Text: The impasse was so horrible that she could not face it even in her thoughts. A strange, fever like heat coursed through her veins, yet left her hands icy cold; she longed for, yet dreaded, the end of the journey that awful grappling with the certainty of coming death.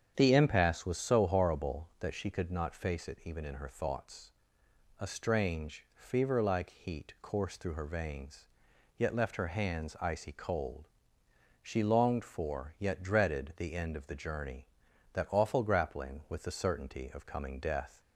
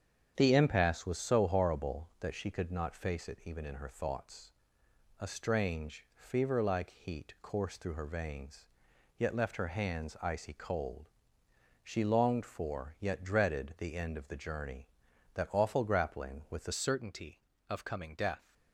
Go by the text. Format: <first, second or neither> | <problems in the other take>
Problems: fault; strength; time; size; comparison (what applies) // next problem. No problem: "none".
first | starts louder than the rest; strong; until 1.3 s; 8 dB; strong in the first // changes voice at "certainty"; from 16.7 s on; 1.8 s long